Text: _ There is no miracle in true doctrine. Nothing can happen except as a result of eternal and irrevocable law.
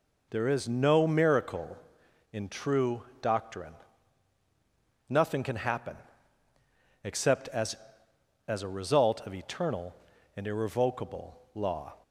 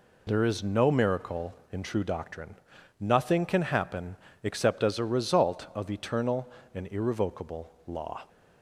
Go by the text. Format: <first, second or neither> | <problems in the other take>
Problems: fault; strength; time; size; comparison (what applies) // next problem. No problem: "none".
second | pauses between "true" and "doctrine"; slight; at 3.0 s; 0.20 s long // pauses between "happen" and "except"; at 5.9 s; 1.0 s long; slight in the second // says "as" twice; at 8.4 s